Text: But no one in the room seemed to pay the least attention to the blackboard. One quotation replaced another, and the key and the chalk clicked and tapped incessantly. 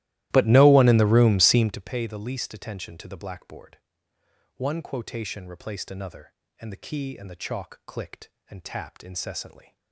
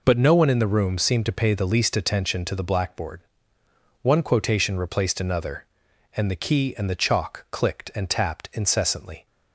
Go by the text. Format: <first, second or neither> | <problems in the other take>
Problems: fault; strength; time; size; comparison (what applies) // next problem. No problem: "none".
second | starts louder than the rest; strong; until 1.9 s; 15.5 dB